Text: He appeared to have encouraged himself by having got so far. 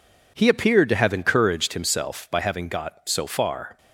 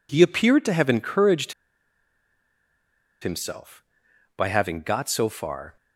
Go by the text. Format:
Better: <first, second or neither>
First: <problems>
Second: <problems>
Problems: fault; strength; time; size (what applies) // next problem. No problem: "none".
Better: first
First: none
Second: pauses between "encouraged" and "himself"; strong; at 1.5 s; 1.6 s long